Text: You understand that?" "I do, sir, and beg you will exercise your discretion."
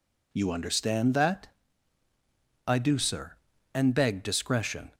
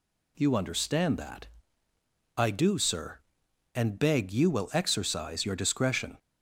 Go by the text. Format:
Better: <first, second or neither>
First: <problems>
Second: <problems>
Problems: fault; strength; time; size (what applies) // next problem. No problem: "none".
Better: second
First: skips "you will exercise your"; at 4.2 s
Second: none